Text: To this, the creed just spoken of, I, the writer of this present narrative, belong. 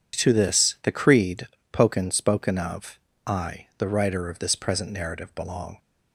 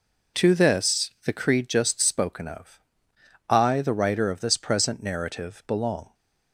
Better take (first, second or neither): second